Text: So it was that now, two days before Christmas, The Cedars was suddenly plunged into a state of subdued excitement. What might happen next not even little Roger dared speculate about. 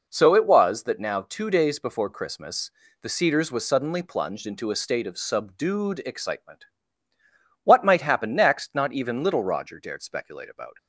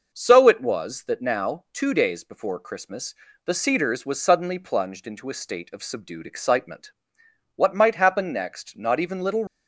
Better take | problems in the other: first | stops before "Roger dared speculate about"; at 9.4 s

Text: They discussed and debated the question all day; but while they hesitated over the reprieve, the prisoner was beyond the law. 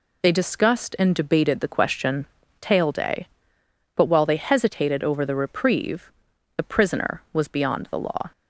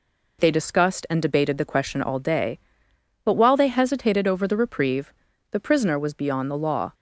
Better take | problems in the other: second | says "tail" for "all"; at 2.5 s

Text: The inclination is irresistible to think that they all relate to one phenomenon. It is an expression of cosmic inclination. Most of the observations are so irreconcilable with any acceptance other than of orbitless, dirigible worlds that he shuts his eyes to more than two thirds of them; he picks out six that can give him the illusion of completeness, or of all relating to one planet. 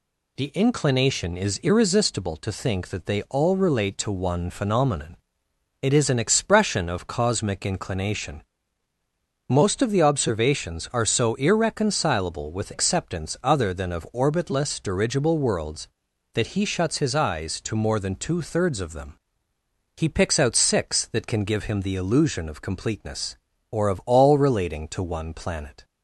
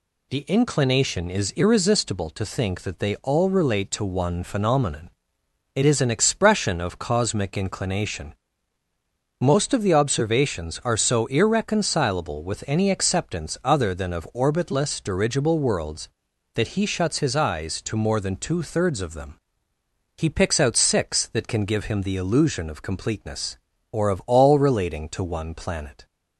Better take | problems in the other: second | skips "any"; at 12.7 s

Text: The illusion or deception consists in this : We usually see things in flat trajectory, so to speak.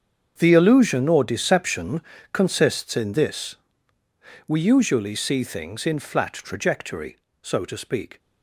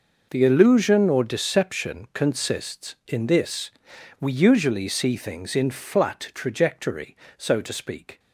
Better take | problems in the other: second | gets quieter; strong; throughout; 16 dB // pauses between "deception" and "consists"; slight; at 2.0 s; 0.32 s long

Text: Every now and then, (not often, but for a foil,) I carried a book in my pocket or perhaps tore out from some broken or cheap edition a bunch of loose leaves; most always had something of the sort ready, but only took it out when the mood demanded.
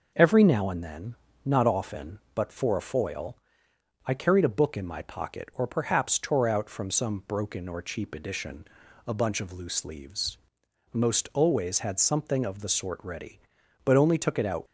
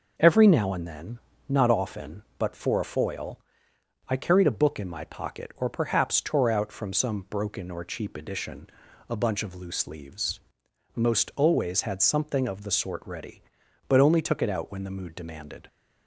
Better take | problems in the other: second | pauses between "edition" and "a"; at 8.6 s; 0.40 s long; also in the second // stops before "when the mood demanded"; at 14.6 s

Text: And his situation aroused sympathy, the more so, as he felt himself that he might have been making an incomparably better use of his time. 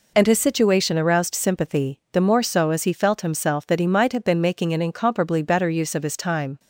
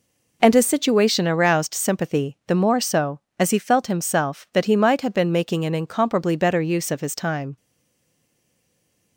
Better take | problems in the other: first | stays silent after the last word; noticeable; from 7.5 s on; 1.6 s long

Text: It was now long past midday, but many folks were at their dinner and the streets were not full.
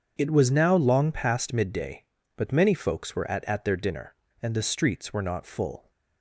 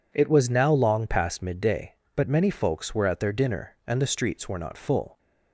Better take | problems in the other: second | starts louder than the rest; strong; until 1.1 s; 7.5 dB // says "at" twice; at 3.4 s

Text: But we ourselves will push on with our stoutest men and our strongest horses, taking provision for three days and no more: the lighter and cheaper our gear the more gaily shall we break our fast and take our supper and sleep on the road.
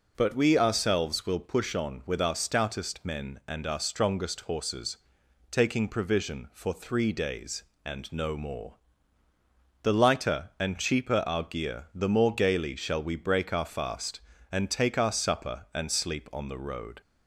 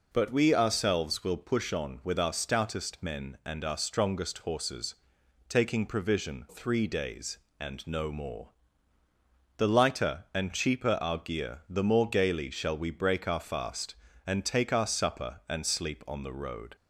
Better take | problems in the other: first | skips "for"; at 6.4 s

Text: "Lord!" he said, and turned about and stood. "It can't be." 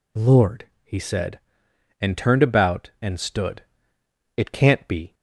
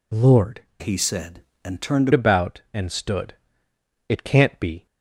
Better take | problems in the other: first | changes voice from "he" to "turned"; from 0.8 to 2.0 s; 1.2 s long

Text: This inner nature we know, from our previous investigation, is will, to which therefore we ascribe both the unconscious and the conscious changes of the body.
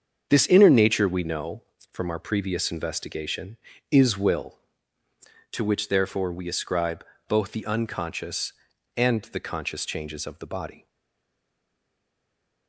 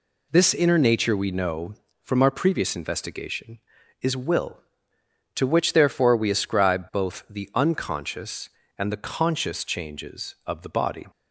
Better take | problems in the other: second | starts louder than the rest; until 1.3 s; 7 dB // pauses between "ascribe" and "both"; slight; at 7.0 s; 0.22 s long // stays silent after the last word; noticeable; from 10.8 s on; 1.8 s long

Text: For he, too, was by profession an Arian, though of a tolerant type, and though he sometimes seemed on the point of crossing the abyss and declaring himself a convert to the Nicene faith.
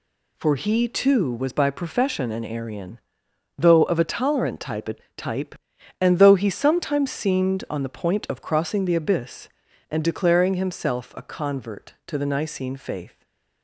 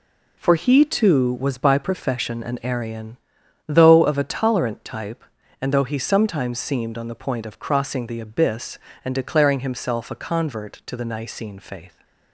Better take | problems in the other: second | says "type" twice; at 5.1 s // stays silent after the last word; slight; from 13.0 s on; 0.6 s long

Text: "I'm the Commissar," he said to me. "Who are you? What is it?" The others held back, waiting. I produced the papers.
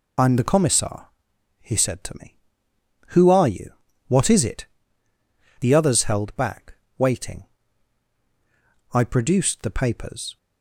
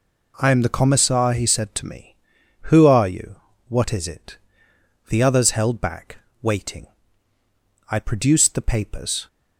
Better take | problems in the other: second | loses the start of "I'm"; at 0.1 s; 40 ms

